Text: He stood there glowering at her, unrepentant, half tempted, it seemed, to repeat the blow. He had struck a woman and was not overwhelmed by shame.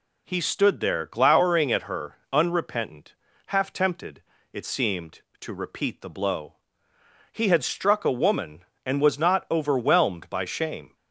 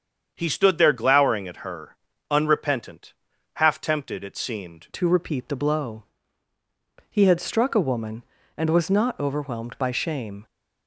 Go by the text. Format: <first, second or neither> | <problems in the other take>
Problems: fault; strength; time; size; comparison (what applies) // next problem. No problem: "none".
first | starts louder than the rest; strong; until 1.3 s; 7.5 dB // changes voice at "to"; from 4.9 s on; 5.5 s long